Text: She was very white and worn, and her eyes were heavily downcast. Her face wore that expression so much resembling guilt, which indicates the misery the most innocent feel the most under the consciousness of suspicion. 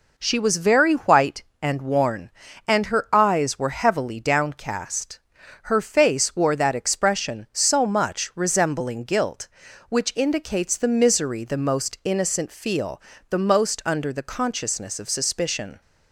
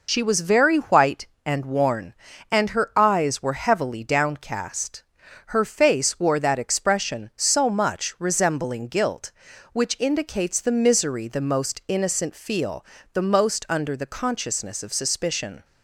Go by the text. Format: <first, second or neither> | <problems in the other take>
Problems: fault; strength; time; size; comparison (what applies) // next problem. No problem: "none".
first | loses the start of "She"; at 0.0 s; 65 ms // pauses between "feel" and "the"; slight; at 12.8 s; 0.28 s long; slight in the first